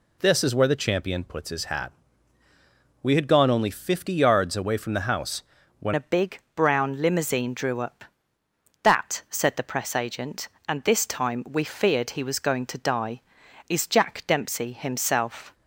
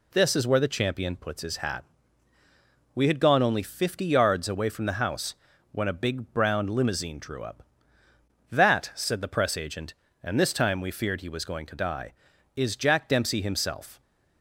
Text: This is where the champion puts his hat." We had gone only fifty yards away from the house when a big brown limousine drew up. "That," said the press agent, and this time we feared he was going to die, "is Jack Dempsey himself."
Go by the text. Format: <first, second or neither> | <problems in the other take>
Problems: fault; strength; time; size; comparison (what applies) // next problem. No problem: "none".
second | pauses between "house" and "when"; slight; at 5.4 s; 0.36 s long; slight in the second // changes voice at "a"; from 5.9 s on; 9.6 s long // pauses between "big" and "brown"; slight; at 6.3 s; 0.16 s long